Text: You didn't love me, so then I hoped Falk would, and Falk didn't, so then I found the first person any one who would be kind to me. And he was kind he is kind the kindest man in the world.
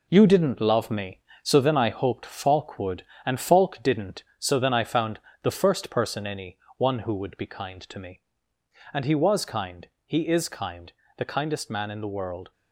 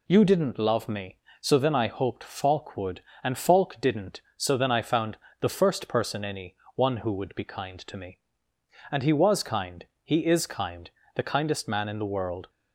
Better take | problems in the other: second | gets quieter; throughout; 7 dB // pauses between "found" and "the"; slight; at 5.1 s; 0.22 s long; slight in the second // pauses between "any" and "one"; slight; at 6.5 s; 0.20 s long; slight in the second // pauses between "kind" and "he"; slight; at 9.8 s; 0.18 s long; slight in the second // pauses between "kind" and "the"; slight; at 10.9 s; 0.24 s long; slight in the second

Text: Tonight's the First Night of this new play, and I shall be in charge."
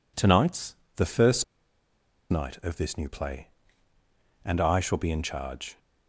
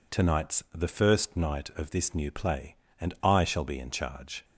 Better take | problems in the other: second | pauses between "Tonight's" and "the"; slight; at 0.7 s; 0.18 s long // pauses between "First" and "Night"; noticeable; at 1.4 s; 0.86 s long

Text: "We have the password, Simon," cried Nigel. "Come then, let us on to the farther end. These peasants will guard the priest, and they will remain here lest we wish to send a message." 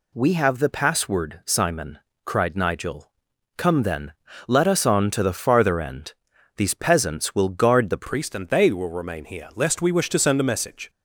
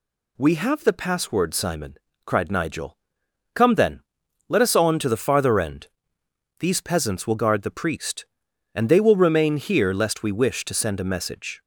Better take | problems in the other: second | changes voice at "priest"; from 8.0 s on; 2.8 s long

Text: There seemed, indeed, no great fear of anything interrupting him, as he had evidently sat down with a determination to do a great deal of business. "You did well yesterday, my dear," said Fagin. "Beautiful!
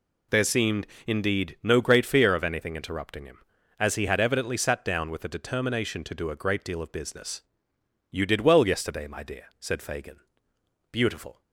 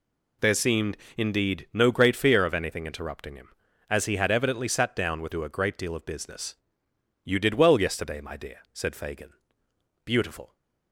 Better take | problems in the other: first | skips "a determination to"; at 5.3 s

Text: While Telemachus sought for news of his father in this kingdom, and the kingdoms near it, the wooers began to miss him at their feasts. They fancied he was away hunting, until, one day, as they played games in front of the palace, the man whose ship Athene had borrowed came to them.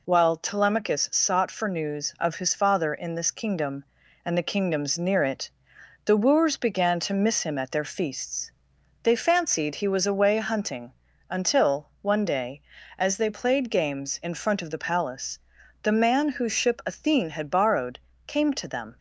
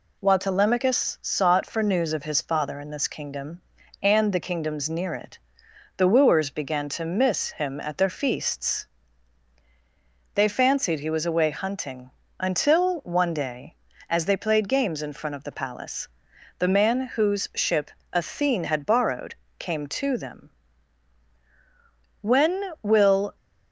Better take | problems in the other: first | pauses between "ship" and "Athene"; slight; at 17.9 s; 0.20 s long // pauses between "borrowed" and "came"; slight; at 19.3 s; 0.24 s long; slight in the first // goes on to say "When will"; noticeable; from 22.2 s on; 1.1 s long

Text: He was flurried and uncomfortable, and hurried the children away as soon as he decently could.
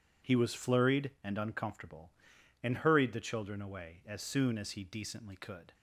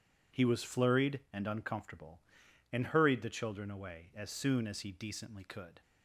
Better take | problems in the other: neither | none

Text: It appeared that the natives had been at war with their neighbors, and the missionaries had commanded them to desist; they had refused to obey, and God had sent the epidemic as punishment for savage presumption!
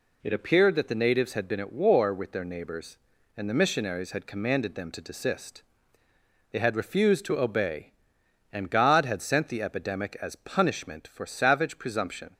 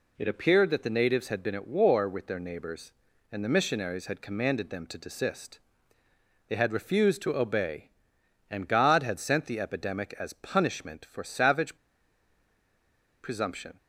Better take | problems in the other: first | pauses between "savage" and "presumption"; strong; at 11.7 s; 1.4 s long

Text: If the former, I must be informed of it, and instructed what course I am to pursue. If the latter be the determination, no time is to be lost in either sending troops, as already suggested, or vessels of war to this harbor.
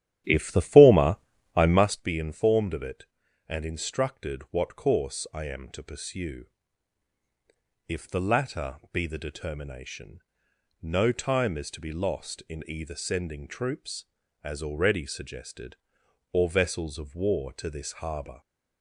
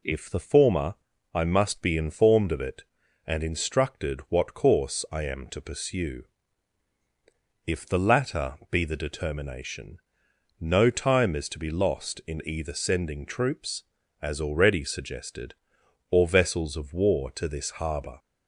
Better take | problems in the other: second | starts louder than the rest; strong; until 2.0 s; 12 dB

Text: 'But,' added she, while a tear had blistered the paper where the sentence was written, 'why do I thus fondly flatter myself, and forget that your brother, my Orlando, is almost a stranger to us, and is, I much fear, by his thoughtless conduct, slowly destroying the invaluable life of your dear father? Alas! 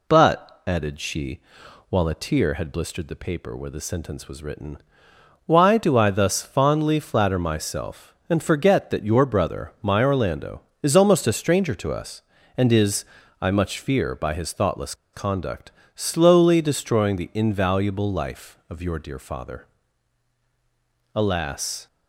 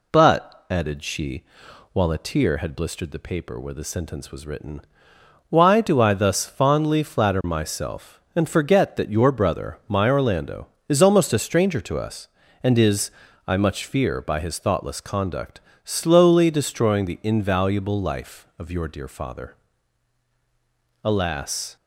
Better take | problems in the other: second | pauses between "thoughtless" and "conduct"; slight; at 14.9 s; 0.19 s long

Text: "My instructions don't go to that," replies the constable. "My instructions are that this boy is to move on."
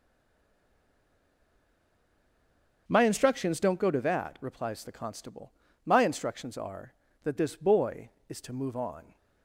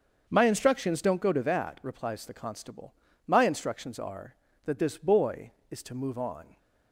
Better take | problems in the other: second | stays silent before the first word; strong; until 2.8 s; 2.8 s long // starts louder than the rest; until 3.8 s; 7 dB; also in the second

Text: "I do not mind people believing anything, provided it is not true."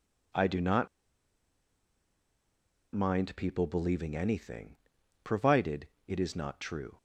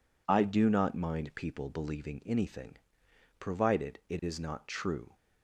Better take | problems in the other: second | pauses between "not" and "mind"; strong; at 0.8 s; 2.0 s long // pauses between "provided" and "it"; slight; at 5.8 s; 0.20 s long

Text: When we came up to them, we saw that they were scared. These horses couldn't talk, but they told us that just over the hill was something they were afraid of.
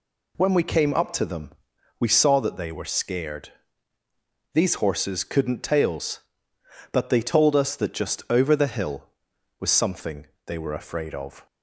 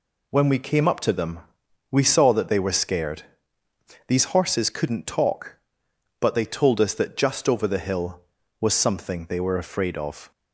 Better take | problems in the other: second | says "tails" for "talk"; at 5.6 s // pauses between "something" and "they"; slight; at 10.2 s; 0.20 s long

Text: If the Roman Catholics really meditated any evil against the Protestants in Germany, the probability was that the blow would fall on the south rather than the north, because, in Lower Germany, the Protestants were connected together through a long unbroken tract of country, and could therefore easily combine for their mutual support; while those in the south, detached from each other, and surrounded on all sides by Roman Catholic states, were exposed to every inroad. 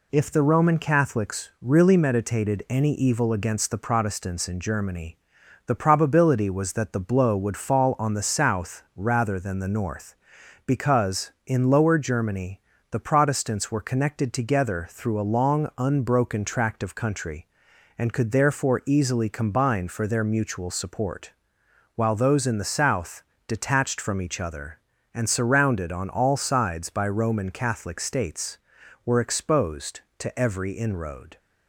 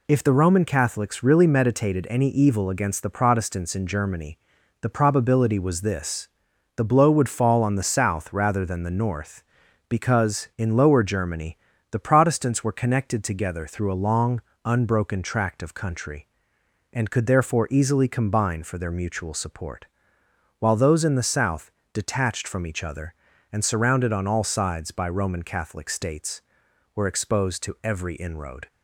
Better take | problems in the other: first | says "this" for "that"; at 5.8 s // pauses between "long" and "unbroken"; slight; at 14.4 s; 0.20 s long

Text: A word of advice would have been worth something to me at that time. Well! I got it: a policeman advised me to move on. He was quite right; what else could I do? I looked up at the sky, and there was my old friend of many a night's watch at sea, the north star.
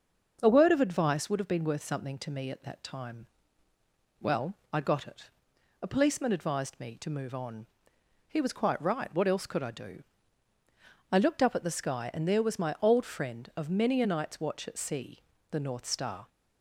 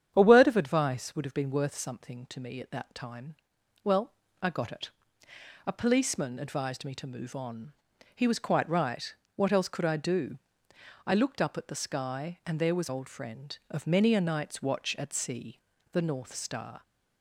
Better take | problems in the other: first | starts louder than the rest; strong; until 1.1 s; 9 dB; also in the first // skips "my"; at 12.8 s

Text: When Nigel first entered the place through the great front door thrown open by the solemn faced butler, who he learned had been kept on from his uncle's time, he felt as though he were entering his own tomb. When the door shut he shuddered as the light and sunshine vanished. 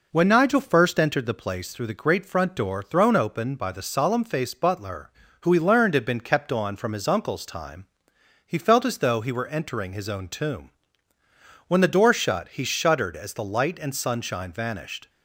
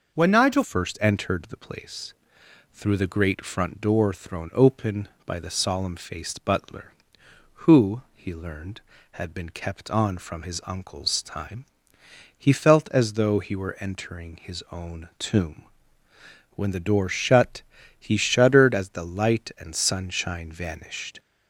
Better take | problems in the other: first | changes voice at "first"; from 0.6 s on; 20.5 s long // pauses between "place" and "through"; noticeable; at 2.1 s; 0.58 s long // pauses between "who" and "he"; slight; at 8.0 s; 0.16 s long // pauses between "shut" and "he"; at 17.6 s; 0.38 s long

